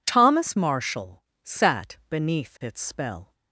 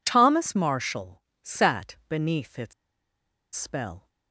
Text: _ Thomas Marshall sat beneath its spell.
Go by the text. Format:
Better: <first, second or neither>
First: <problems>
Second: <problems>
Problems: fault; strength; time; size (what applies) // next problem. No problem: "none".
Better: first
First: pauses between "Marshall" and "sat"; slight; at 1.2 s; 0.20 s long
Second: pauses between "Marshall" and "sat"; slight; at 1.2 s; 0.20 s long // pauses between "its" and "spell"; noticeable; at 2.7 s; 0.82 s long